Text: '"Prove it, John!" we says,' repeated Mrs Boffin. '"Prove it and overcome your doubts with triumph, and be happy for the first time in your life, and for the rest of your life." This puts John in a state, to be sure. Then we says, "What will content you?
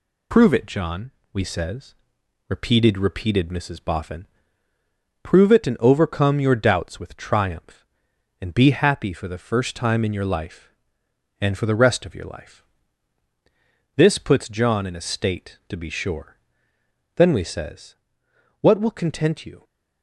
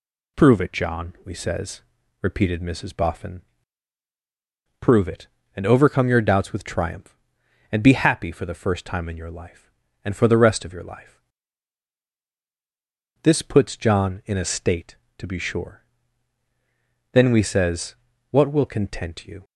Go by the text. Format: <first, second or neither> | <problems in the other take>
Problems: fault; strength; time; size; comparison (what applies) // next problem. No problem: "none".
second | says "repeated" twice; at 2.9 s